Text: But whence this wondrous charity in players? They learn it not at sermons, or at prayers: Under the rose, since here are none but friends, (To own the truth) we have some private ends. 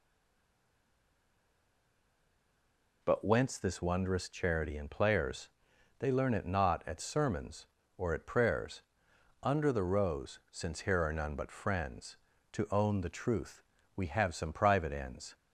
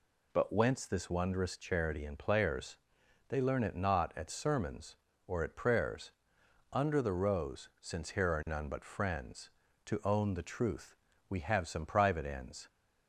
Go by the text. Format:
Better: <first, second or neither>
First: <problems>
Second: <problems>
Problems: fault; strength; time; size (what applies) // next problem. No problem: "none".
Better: second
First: stays silent before the first word; strong; until 3.0 s; 3.0 s long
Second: none